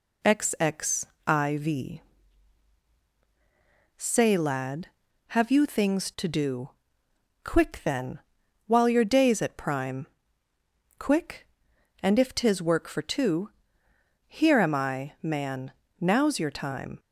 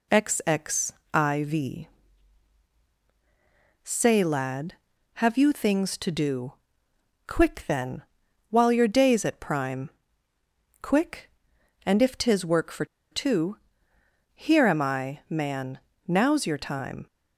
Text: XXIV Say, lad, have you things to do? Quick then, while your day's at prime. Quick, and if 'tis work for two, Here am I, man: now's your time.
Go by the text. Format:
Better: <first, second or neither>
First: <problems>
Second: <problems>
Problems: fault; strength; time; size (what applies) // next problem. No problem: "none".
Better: first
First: pauses between "XXIV" and "Say"; strong; at 1.9 s; 1.9 s long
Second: pauses between "XXIV" and "Say"; strong; at 1.8 s; 1.9 s long // pauses between "for" and "two"; slight; at 12.8 s; 0.25 s long